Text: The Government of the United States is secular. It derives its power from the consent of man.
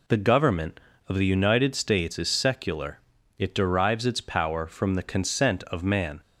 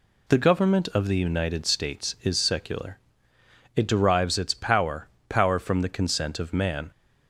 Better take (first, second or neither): first